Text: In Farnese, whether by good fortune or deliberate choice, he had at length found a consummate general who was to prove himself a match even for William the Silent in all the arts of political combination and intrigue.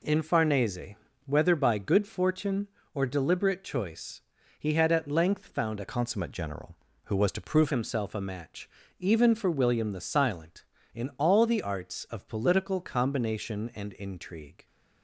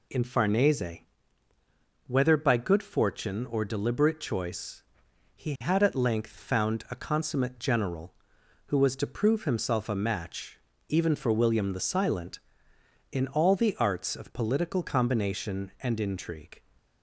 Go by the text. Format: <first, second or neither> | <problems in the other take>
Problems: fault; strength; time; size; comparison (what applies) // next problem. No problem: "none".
second | changes voice from "consummate" to "prove"; from 5.8 to 7.7 s; 1.9 s long // pauses between "match" and "even"; slight; at 8.6 s; 0.30 s long; slight in the second